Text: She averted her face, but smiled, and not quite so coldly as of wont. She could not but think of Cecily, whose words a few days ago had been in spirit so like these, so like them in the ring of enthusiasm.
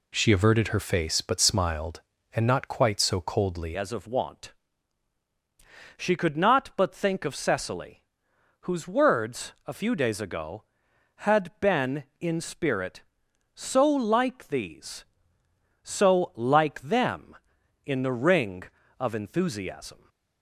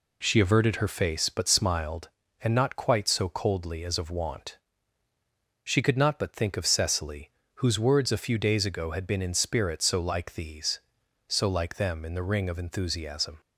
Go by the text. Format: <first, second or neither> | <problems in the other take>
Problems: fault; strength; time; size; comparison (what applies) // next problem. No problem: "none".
second | changes voice at "as"; from 3.7 s on; 16.3 s long